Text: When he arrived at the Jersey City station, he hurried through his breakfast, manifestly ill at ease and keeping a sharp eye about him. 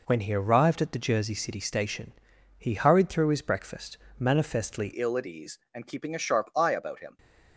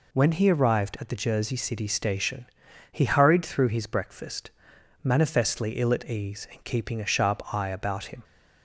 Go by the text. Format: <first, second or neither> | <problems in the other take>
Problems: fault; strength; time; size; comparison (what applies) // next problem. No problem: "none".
second | changes voice at "ill"; from 4.9 s on; 2.2 s long